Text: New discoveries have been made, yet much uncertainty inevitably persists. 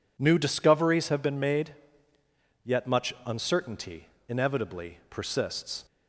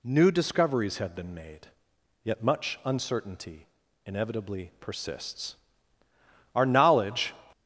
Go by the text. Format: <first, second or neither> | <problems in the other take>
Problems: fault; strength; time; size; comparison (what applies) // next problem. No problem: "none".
first | pauses between "uncertainty" and "inevitably"; at 3.6 s; 0.38 s long; slight in the first // goes on to say "Our knowledge"; noticeable; from 6.5 s on; 0.78 s long